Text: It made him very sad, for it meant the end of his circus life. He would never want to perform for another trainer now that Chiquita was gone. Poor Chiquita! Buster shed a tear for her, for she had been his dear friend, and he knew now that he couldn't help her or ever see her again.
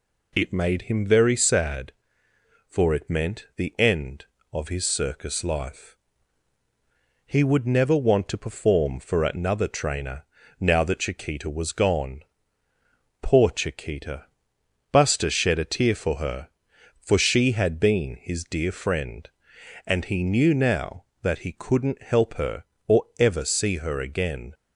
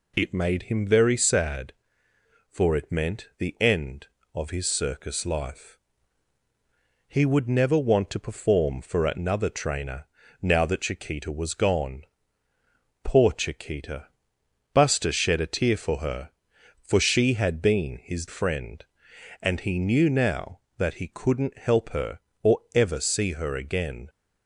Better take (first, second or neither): first